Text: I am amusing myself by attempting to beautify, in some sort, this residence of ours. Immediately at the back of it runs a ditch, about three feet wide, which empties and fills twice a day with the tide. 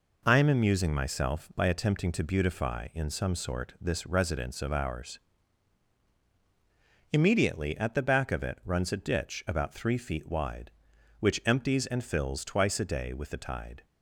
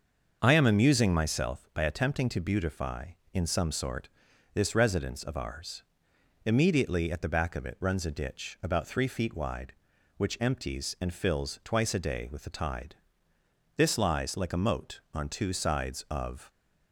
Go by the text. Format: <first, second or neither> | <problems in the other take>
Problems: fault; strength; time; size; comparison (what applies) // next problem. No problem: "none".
first | starts louder than the rest; until 1.4 s; 6.5 dB // goes on to say "This lies like a moat on two sides of"; strong; from 13.7 s on; 2.7 s long